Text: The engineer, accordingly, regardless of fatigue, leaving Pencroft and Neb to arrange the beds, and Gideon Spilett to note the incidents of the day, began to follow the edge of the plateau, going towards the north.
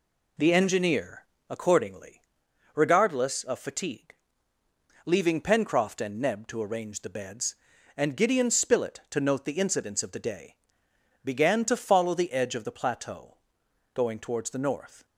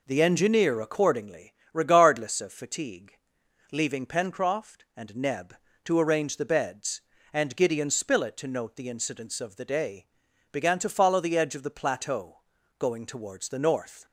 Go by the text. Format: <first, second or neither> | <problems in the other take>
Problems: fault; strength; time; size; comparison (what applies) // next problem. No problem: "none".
first | starts louder than the rest; until 1.3 s; 4 dB